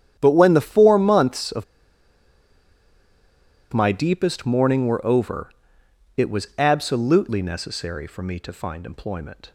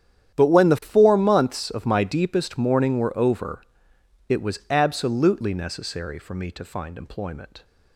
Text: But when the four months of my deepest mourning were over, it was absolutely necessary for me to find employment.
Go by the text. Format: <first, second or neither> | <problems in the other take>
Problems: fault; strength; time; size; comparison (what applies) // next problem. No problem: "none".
second | starts louder than the rest; strong; until 1.2 s; 10 dB; strong in the second // pauses between "of" and "my"; strong; at 1.6 s; 2.0 s long